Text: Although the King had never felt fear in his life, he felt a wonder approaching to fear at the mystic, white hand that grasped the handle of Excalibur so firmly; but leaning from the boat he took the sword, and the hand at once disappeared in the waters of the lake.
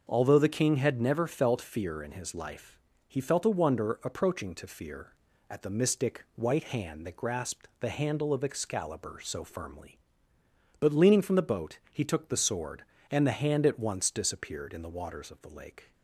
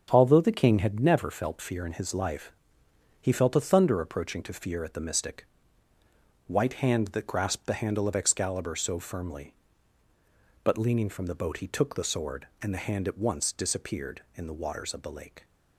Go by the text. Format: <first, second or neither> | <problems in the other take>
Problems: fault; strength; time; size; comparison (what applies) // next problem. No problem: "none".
first | starts louder than the rest; strong; until 1.1 s; 7.5 dB; noticeable in the first // says "thunder" for "wonder"; at 3.6 s